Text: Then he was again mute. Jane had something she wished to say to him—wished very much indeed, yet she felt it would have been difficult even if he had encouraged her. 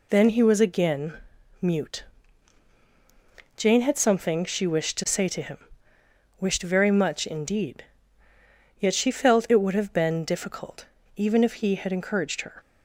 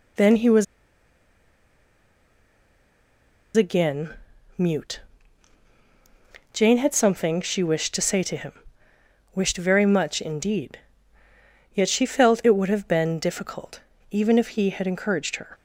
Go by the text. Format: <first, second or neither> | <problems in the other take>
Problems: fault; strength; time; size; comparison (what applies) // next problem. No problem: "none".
first | pauses between "was" and "again"; strong; at 0.6 s; 2.9 s long // pauses between "again" and "mute"; at 4.1 s; 0.44 s long; also in the first // pauses between "difficult" and "even"; slight; at 13.7 s; 0.32 s long; slight in the first